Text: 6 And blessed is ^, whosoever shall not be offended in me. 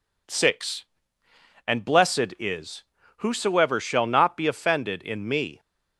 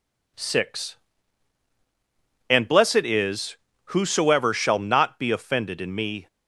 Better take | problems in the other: neither | none

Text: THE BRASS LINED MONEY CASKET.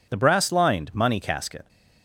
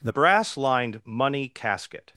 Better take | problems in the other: first | changes voice at "BRASS"; from 0.0 s on; 2.1 s long

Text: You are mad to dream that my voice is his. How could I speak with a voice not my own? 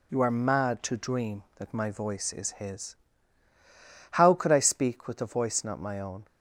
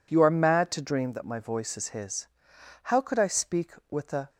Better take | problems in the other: first | stops before "voice not my own"; at 4.2 s

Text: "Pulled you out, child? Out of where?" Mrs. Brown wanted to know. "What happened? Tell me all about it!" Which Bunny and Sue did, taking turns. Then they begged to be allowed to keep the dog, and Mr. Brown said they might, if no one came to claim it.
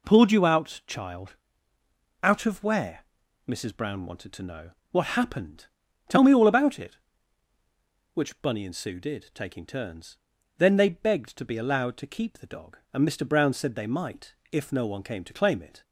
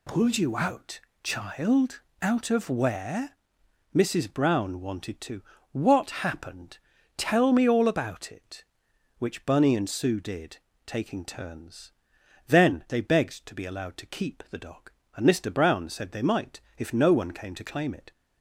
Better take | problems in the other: first | skips "know"; at 5.5 s

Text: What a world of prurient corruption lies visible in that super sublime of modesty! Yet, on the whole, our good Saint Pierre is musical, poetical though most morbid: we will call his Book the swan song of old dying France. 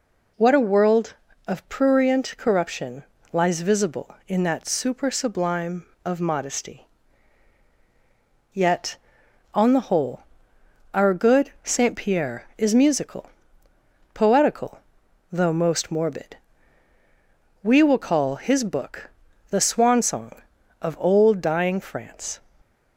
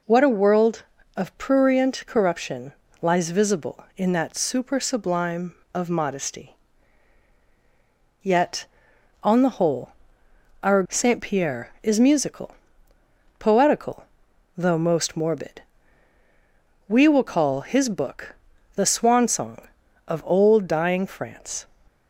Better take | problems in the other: first | pauses between "corruption" and "lies"; slight; at 2.7 s; 0.28 s long; slight in the first // skips "good"; at 10.8 s // pauses between "poetical" and "though"; noticeable; at 14.0 s; 0.52 s long; noticeable in the first // pauses between "Book" and "the"; at 18.3 s; 0.40 s long; also in the first

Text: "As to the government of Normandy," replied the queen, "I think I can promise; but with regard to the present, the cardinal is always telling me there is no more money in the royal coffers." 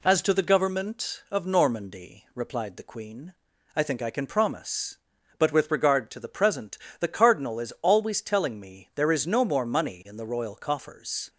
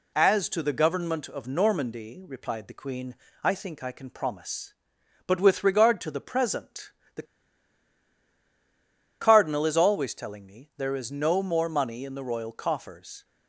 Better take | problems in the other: first | pauses between "the" and "cardinal"; strong; at 7.2 s; 1.9 s long

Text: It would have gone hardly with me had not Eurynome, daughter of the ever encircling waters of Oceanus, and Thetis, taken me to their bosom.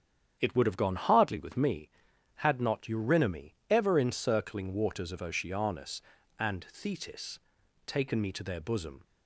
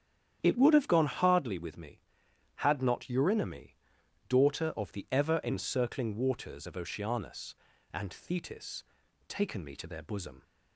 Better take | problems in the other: second | starts louder than the rest; strong; until 1.4 s; 9 dB; strong in the second // skips "daughter of the"; at 3.6 s

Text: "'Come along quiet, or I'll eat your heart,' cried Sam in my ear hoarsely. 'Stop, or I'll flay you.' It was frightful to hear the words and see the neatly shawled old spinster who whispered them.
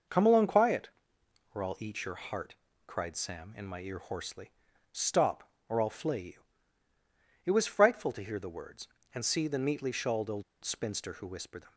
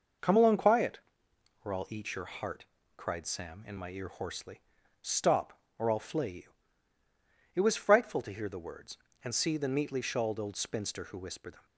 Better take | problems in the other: second | pauses between "old" and "spinster"; slight; at 10.4 s; 0.20 s long

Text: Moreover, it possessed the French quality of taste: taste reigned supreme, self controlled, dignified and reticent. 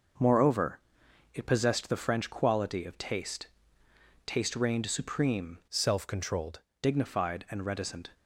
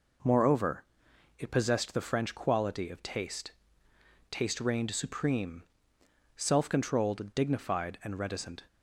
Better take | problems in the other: second | changes voice from "self" to "controlled"; from 5.6 to 6.6 s; 1.0 s long

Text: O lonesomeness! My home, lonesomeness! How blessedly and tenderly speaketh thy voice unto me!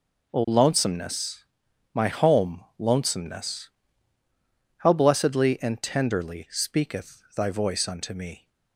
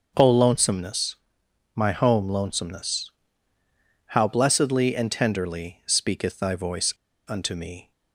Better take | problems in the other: first | starts louder than the rest; noticeable; until 1.1 s; 6 dB // pauses between "voice" and "unto"; at 6.9 s; 0.36 s long

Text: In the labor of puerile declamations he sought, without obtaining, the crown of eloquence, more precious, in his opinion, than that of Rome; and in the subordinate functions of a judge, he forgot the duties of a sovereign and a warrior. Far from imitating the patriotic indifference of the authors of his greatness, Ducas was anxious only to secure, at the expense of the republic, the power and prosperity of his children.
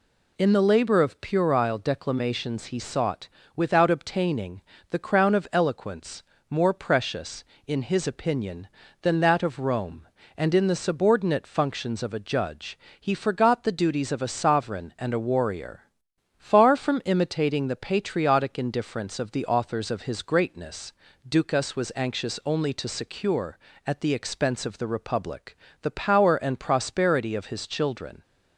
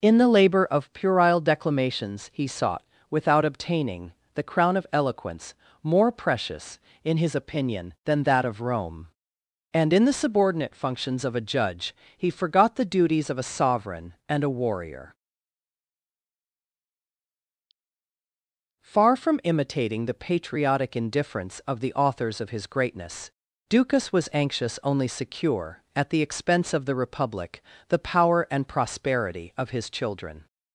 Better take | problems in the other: first | skips "to"; at 25.0 s

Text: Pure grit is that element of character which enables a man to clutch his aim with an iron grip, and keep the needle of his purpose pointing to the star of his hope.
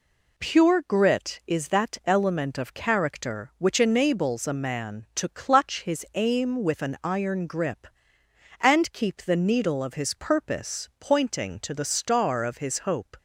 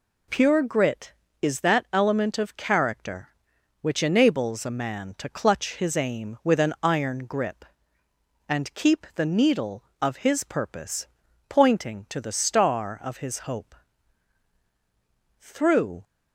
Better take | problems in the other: first | pauses between "purpose" and "pointing"; at 11.0 s; 0.40 s long // goes on to say "Through"; noticeable; from 15.4 s on; 0.62 s long

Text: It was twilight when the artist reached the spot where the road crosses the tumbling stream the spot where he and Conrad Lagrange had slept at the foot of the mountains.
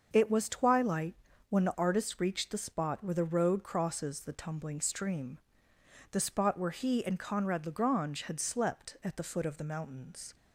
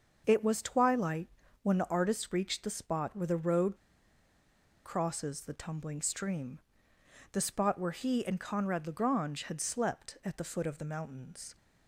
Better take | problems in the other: first | starts louder than the rest; until 1.2 s; 6 dB; also in the first // pauses between "twilight" and "when"; slight; at 1.2 s; 0.34 s long; slight in the first // pauses between "road" and "crosses"; at 3.7 s; 1.1 s long // pauses between "stream" and "the"; noticeable; at 6.5 s; 0.72 s long; noticeable in the first

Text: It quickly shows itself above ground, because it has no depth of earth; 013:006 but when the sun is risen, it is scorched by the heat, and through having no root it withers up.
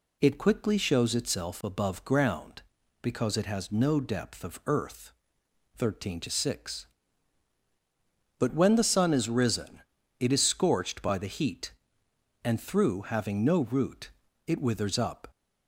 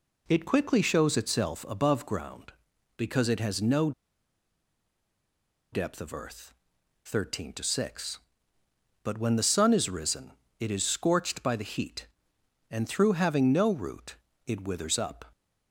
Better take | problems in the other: first | pauses between "no" and "depth"; strong; at 3.9 s; 1.8 s long // pauses between "root" and "it"; slight; at 14.1 s; 0.32 s long; slight in the first

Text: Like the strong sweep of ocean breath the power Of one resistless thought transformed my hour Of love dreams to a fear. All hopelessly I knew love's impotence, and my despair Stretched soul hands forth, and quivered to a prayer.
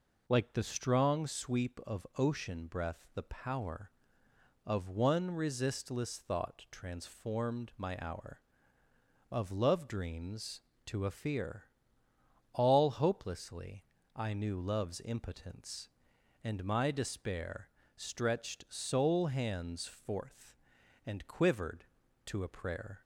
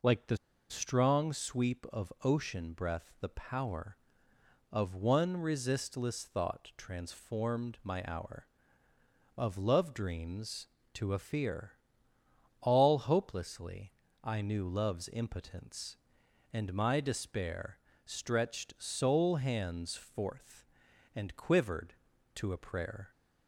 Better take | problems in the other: first | pauses between "the" and "strong"; slight; at 0.3 s; 0.33 s long // pauses between "hopelessly" and "I"; slight; at 13.9 s; 0.30 s long; slight in the first // pauses between "despair" and "Stretched"; slight; at 17.7 s; 0.26 s long; slight in the first

